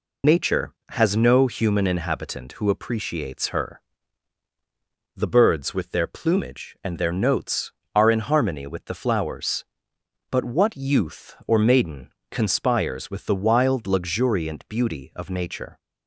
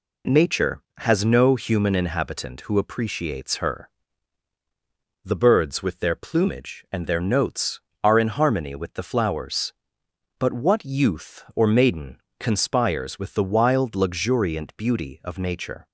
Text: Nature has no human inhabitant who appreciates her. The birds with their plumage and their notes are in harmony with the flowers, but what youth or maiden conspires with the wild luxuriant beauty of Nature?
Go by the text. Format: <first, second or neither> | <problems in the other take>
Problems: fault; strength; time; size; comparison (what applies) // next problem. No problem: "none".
second | loses the start of "Nature"; at 0.2 s; 75 ms // pauses between "maiden" and "conspires"; slight; at 12.0 s; 0.24 s long; slight in the second